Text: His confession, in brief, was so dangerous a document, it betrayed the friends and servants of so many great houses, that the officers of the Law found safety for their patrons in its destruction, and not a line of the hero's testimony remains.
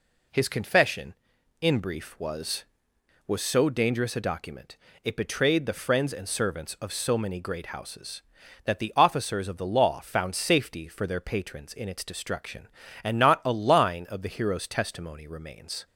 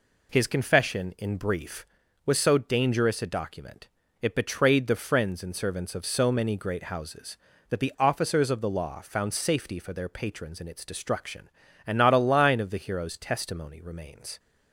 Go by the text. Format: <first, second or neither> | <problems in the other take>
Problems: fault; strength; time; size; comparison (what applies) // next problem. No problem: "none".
second | says "was" twice; at 3.2 s